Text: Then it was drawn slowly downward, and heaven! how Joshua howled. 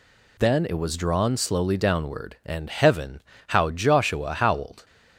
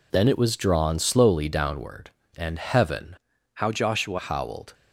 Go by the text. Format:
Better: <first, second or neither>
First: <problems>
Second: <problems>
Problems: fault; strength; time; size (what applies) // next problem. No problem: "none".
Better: first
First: none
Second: changes voice from "how" to "Joshua"; from 3.5 to 4.1 s; 0.6 s long